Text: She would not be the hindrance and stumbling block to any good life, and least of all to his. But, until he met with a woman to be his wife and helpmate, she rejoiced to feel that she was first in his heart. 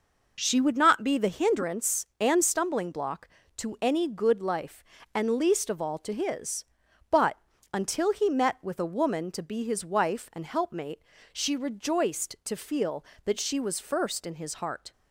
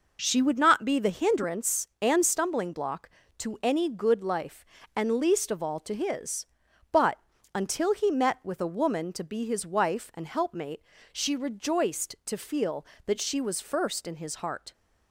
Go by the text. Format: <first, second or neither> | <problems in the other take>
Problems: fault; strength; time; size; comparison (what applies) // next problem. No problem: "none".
neither | none